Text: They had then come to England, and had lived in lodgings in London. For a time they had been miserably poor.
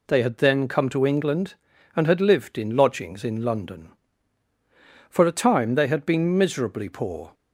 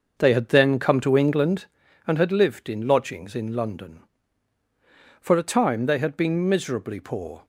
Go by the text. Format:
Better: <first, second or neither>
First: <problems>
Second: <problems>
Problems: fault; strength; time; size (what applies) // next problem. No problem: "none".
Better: first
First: none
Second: starts louder than the rest; noticeable; until 1.9 s; 6 dB